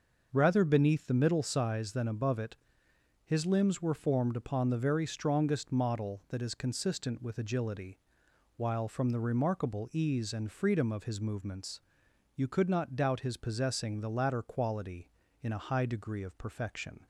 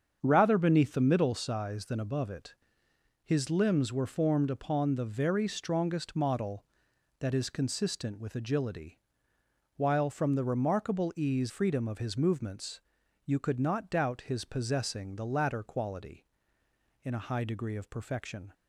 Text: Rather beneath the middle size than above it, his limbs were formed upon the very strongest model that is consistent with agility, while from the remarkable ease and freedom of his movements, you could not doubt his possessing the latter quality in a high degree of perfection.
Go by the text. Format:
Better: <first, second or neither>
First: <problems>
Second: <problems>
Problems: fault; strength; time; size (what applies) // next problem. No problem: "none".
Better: first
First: starts louder than the rest; noticeable; until 1.3 s; 6 dB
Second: starts louder than the rest; strong; until 1.2 s; 7.5 dB // skips "and"; at 11.4 s